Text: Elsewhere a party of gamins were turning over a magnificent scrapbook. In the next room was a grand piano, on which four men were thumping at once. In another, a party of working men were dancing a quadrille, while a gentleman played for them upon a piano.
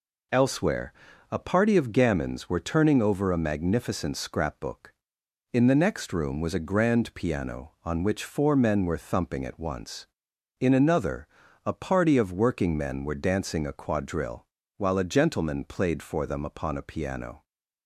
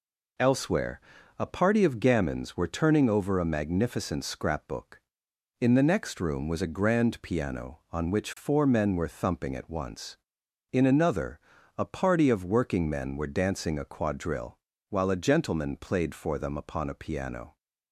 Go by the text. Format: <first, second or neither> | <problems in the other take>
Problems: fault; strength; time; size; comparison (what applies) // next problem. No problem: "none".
neither | pauses between "Elsewhere" and "a"; the same in both